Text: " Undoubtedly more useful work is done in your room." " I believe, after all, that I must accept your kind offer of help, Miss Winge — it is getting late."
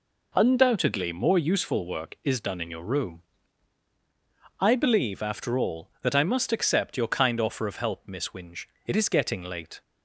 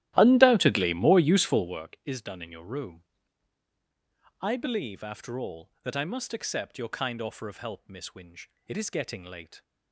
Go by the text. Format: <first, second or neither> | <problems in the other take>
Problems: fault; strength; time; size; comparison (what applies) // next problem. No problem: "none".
first | starts louder than the rest; strong; until 1.9 s; 13.5 dB